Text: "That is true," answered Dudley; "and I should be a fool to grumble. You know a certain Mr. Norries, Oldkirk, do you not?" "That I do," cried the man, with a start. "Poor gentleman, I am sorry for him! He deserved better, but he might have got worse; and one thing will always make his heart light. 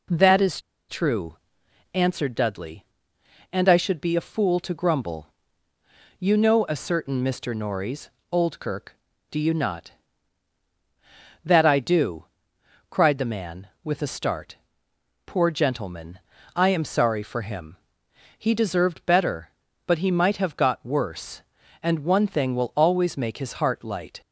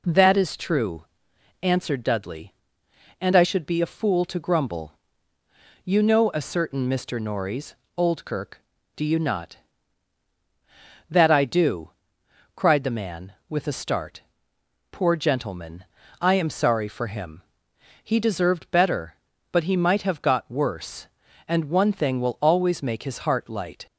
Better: second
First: pauses between "is" and "true"; slight; at 0.5 s; 0.29 s long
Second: none

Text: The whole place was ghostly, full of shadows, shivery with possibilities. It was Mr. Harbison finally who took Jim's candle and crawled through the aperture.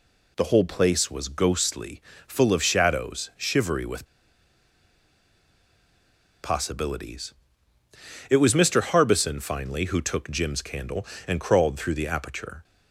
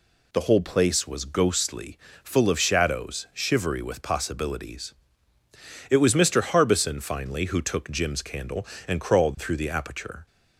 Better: second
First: pauses between "with" and "possibilities"; strong; at 4.0 s; 2.3 s long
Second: none

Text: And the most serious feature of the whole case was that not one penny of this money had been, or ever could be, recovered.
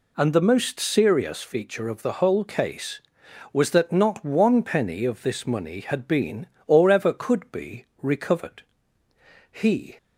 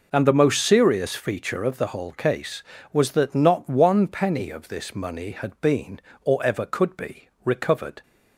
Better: second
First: goes on to say "He"; slight; from 9.5 s on; 0.46 s long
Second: none

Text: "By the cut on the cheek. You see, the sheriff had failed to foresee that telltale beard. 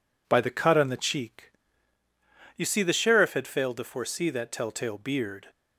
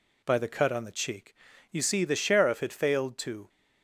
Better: first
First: none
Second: stops before "foresee that telltale beard"; at 3.4 s

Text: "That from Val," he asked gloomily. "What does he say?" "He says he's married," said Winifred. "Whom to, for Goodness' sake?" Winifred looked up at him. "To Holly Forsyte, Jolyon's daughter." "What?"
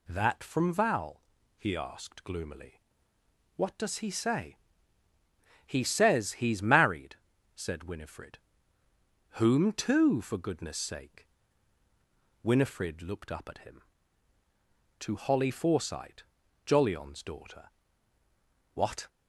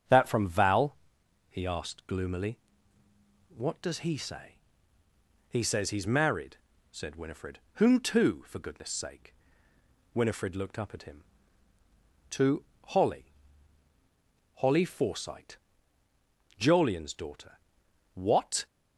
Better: first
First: none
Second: starts louder than the rest; strong; until 1.6 s; 7.5 dB // pauses between "To" and "Holly"; slight; at 12.6 s; 0.20 s long // says "Holly" twice; at 14.5 s

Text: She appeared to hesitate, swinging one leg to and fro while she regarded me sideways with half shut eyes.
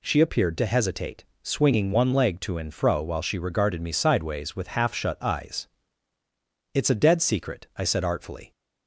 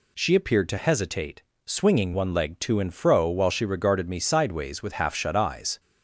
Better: second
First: goes on to say "It's a dead secret I said artfully"; strong; from 6.7 s on; 1.7 s long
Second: none

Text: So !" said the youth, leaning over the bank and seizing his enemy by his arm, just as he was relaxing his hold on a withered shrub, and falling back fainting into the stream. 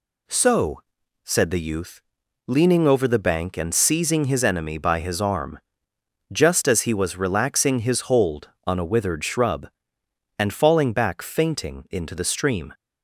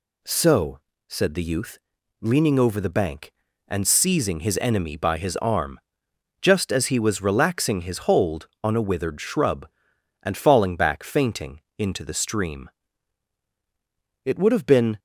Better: first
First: none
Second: pauses between "fainting" and "into"; slight; at 11.6 s; 0.18 s long // goes on to say "It would have been"; noticeable; from 14.2 s on; 0.74 s long

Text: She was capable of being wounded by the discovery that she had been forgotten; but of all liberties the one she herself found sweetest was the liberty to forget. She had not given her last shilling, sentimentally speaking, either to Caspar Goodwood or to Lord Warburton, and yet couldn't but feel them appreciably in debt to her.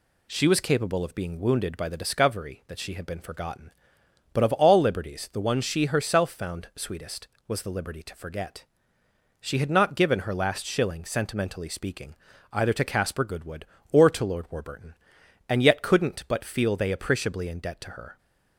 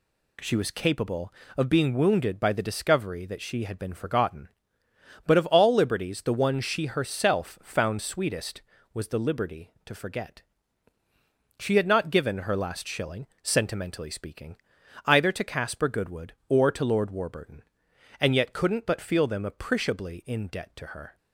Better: second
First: says "they" for "them"; at 16.7 s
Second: none

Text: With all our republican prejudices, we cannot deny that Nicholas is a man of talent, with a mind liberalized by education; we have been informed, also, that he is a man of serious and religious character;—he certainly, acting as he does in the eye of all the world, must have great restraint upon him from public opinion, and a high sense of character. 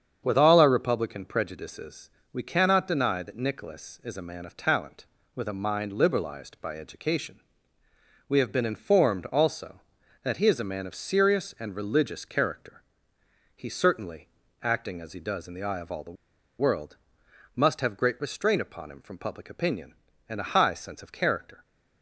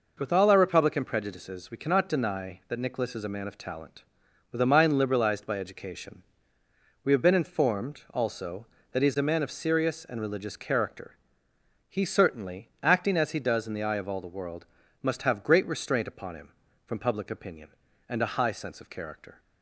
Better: second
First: starts louder than the rest; strong; until 1.2 s; 7.5 dB // pauses between "the" and "world"; at 16.1 s; 0.45 s long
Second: none

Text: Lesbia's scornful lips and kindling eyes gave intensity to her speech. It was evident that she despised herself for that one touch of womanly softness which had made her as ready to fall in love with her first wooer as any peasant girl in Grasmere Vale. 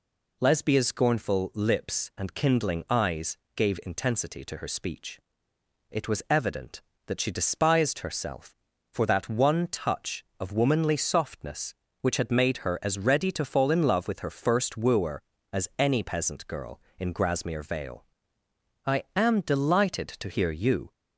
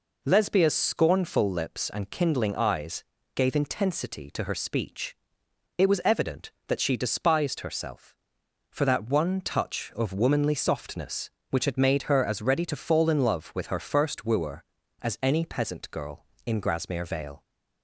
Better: second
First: pauses between "eyes" and "gave"; slight; at 3.3 s; 0.20 s long // goes on to say "I am delighted to hear you"; strong; from 18.8 s on; 2.0 s long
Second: pauses between "eyes" and "gave"; slight; at 3.0 s; 0.30 s long

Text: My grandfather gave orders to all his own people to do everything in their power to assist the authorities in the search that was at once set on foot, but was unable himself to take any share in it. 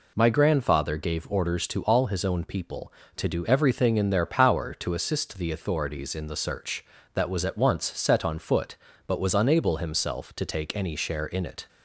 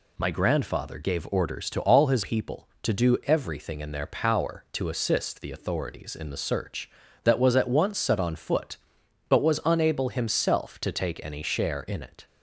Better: first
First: none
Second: skips "own"; at 2.2 s

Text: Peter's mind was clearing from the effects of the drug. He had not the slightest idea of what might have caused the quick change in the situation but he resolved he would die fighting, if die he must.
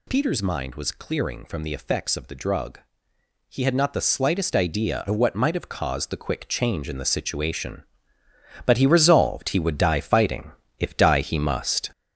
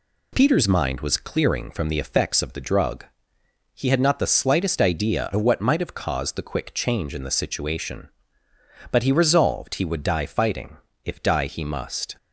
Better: second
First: gets louder; throughout; 6 dB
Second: none

